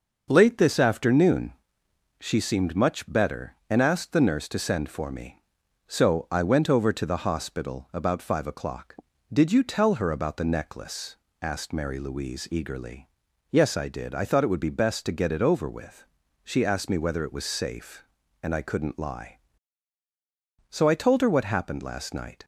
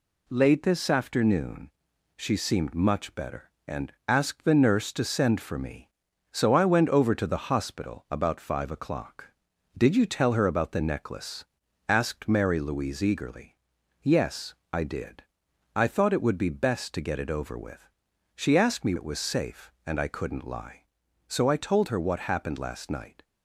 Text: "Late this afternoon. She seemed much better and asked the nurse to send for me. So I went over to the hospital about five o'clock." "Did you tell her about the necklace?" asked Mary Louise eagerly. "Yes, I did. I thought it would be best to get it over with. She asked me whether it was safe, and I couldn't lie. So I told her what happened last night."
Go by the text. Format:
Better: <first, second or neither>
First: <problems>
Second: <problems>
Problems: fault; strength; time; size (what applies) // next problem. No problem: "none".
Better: first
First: none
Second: pauses between "and" and "asked"; slight; at 3.9 s; 0.16 s long // skips "whether"; at 18.9 s